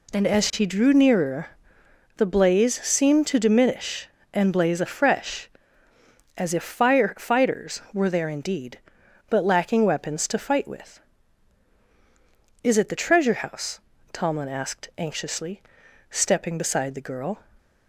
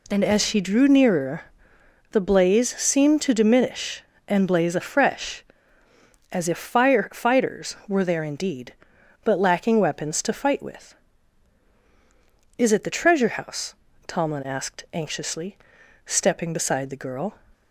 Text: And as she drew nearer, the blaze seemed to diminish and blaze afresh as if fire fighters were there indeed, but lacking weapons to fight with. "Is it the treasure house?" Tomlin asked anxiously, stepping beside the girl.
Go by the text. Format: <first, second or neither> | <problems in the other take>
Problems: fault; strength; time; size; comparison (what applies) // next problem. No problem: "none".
neither | none